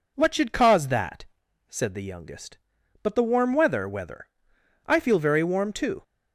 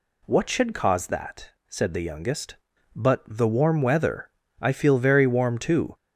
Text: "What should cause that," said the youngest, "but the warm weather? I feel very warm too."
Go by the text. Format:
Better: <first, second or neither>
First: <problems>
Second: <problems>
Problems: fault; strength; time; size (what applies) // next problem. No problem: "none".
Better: second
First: says "weather" twice; at 3.8 s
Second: none